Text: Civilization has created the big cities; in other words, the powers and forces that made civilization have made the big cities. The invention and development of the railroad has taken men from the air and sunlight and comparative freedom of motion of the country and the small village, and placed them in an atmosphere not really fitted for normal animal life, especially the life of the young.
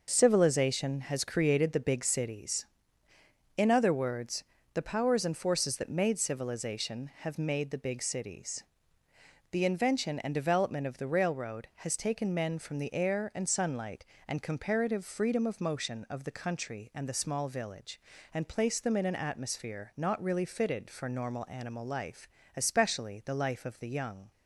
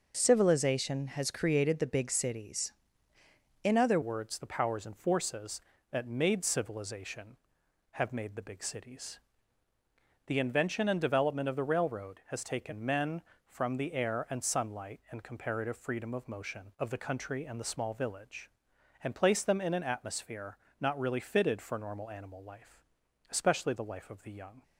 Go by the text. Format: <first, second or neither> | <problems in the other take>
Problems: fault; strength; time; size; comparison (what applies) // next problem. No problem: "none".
first | changes voice at "words"; from 4.0 s on; 20.6 s long // pauses between "atmosphere" and "not"; slight; at 20.5 s; 0.22 s long